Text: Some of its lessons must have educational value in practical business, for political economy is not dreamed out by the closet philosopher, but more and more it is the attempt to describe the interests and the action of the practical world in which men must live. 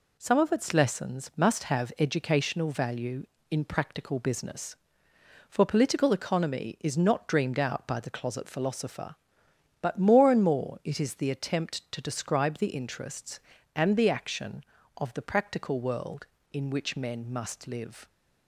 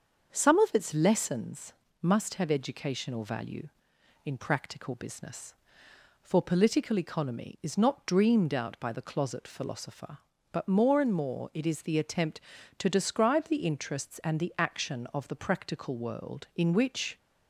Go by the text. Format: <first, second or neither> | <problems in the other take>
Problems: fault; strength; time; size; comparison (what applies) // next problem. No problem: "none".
first | starts louder than the rest; until 1.3 s; 6.5 dB // pauses between "lessons" and "must"; slight; at 1.7 s; 0.28 s long // stops before "men must live"; at 17.1 s